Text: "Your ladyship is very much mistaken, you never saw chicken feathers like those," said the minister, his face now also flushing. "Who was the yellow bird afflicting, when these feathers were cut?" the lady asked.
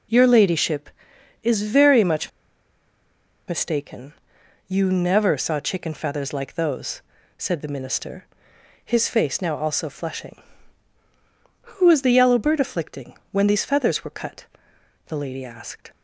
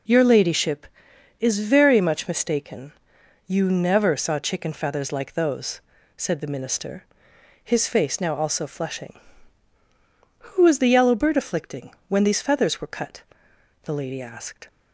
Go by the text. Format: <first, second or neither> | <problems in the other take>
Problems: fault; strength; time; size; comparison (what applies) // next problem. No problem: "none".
second | pauses between "much" and "mistaken"; at 2.2 s; 1.1 s long